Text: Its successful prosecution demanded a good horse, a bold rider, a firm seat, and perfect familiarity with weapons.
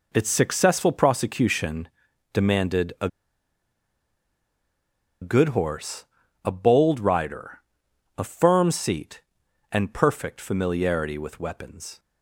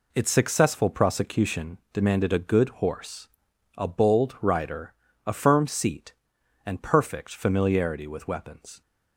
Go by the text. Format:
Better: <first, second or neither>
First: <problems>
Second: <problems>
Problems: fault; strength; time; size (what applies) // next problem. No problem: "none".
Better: second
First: pauses between "prosecution" and "demanded"; noticeable; at 1.8 s; 0.46 s long // pauses between "a" and "good"; strong; at 3.0 s; 2.1 s long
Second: none